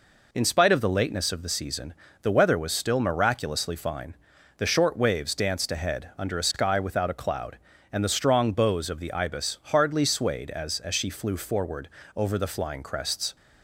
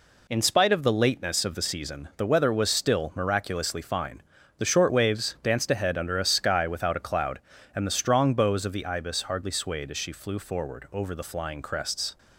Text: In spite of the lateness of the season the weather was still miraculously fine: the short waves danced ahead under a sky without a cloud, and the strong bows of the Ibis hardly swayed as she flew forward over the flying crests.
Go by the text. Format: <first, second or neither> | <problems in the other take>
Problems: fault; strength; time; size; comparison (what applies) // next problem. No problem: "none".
second | pauses between "season" and "the"; slight; at 1.9 s; 0.28 s long // says "as" twice; at 10.7 s // pauses between "forward" and "over"; slight; at 11.8 s; 0.28 s long